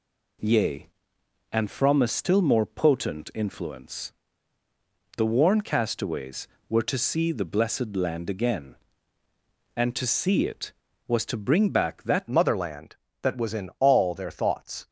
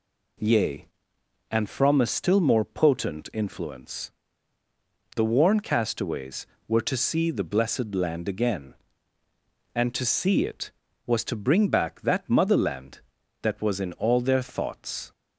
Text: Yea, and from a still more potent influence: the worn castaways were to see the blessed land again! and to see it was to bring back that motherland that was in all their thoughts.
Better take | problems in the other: second | changes voice at "motherland"; from 12.2 s on; 2.6 s long

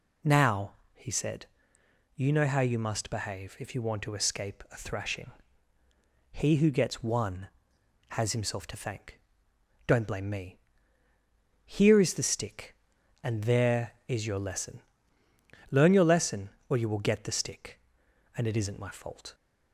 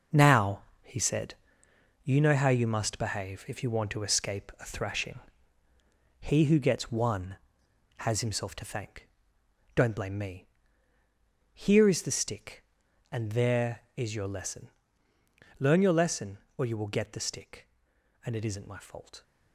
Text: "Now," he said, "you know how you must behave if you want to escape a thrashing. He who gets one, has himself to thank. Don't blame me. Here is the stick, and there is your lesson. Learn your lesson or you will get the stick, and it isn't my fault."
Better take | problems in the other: first | gets quieter; strong; throughout; 8.5 dB

